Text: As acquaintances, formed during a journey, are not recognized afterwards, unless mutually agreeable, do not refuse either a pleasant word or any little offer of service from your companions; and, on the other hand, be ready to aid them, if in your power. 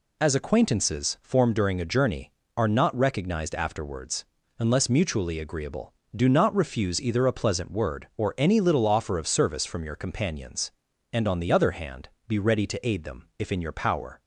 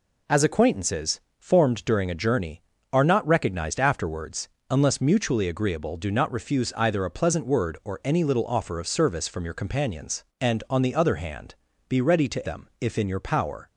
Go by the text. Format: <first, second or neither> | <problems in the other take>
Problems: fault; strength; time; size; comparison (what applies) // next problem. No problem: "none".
first | skips "aid"; at 12.4 s